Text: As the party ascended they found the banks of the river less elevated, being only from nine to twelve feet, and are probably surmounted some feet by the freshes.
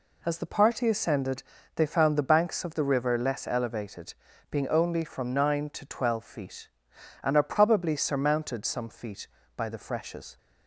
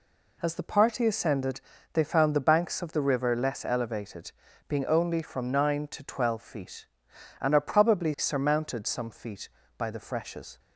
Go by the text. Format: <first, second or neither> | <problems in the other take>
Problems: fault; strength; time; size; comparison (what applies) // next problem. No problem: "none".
neither | pauses between "ascended" and "they"; slight; the same in both